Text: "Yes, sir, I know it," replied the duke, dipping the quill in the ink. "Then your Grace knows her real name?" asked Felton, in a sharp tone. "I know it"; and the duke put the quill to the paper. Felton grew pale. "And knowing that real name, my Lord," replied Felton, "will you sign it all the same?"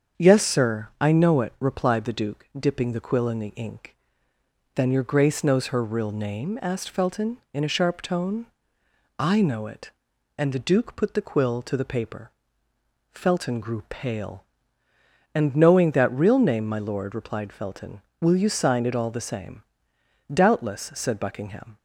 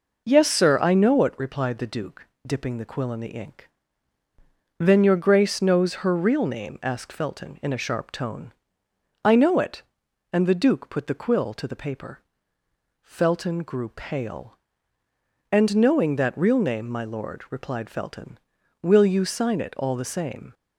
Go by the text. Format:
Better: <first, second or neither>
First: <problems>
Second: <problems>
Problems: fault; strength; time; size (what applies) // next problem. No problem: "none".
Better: second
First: starts louder than the rest; strong; until 1.2 s; 7 dB // goes on to say "Doubtless said Buckingham"; from 20.3 s on; 1.4 s long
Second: none